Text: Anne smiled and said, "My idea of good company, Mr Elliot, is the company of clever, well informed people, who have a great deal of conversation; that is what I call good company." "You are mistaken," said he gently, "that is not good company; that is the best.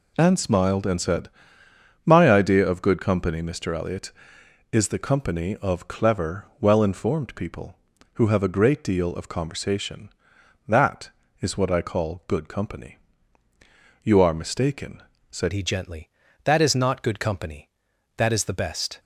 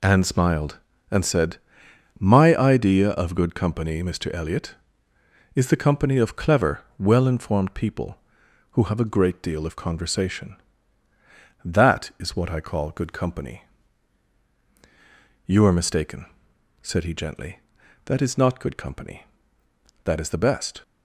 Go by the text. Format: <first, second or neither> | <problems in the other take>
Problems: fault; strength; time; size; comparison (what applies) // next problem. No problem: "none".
second | changes voice at "he"; from 15.5 s on; 3.4 s long